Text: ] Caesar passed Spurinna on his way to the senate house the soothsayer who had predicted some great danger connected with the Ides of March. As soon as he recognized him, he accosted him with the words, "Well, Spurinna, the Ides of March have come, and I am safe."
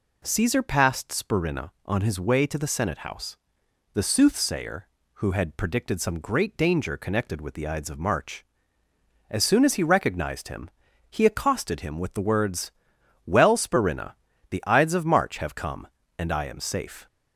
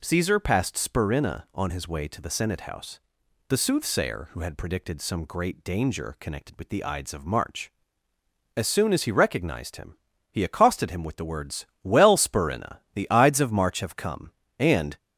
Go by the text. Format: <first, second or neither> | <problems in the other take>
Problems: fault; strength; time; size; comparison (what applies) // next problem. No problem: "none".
first | pauses between "house" and "the"; noticeable; at 2.9 s; 0.50 s long; noticeable in the first // stops before "I am safe"; at 14.9 s